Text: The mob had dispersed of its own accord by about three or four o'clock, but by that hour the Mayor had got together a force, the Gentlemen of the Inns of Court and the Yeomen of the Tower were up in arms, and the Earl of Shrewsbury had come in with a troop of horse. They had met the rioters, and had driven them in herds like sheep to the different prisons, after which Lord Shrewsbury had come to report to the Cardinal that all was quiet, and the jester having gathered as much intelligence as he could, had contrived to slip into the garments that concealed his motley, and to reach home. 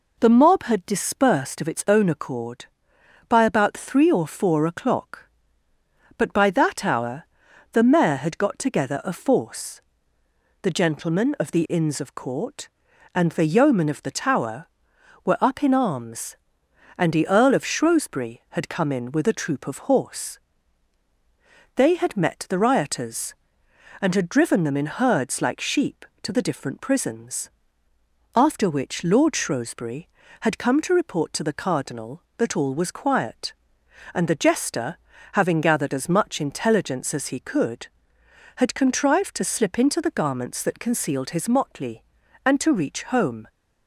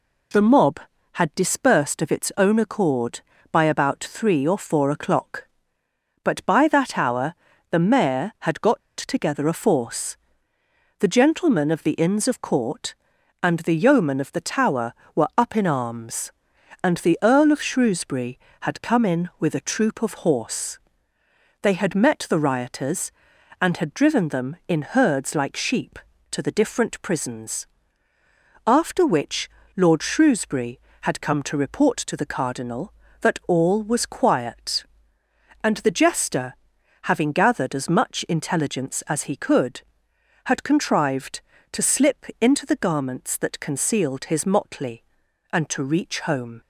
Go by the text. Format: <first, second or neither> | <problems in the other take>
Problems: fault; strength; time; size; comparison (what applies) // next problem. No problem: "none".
first | pauses between "hour" and "the"; slight; at 7.3 s; 0.36 s long; noticeable in the first // pauses between "got" and "together"; slight; at 8.7 s; 0.17 s long // pauses between "which" and "Lord"; slight; at 29.5 s; 0.26 s long // pauses between "jester" and "having"; noticeable; at 36.5 s; 0.48 s long; slight in the first // pauses between "slip" and "into"; slight; at 42.2 s; 0.16 s long